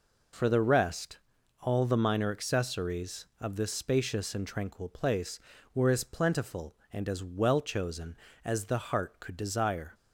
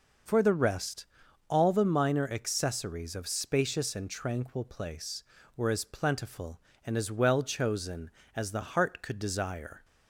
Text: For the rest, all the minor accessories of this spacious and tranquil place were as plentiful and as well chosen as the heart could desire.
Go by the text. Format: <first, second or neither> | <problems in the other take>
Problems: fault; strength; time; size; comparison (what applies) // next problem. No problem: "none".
first | skips "this"; at 3.2 s